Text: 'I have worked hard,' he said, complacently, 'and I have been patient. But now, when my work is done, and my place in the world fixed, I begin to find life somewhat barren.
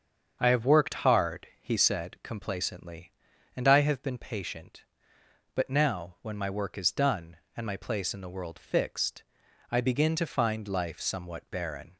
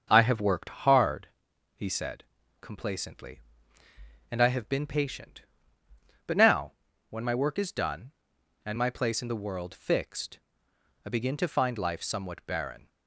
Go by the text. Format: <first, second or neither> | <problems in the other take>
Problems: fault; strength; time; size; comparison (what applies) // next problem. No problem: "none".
neither | starts louder than the rest; the same in both